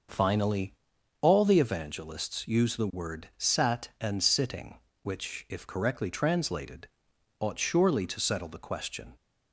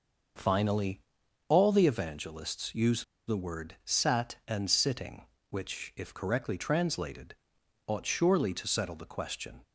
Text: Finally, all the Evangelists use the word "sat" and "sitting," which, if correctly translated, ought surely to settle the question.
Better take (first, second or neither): first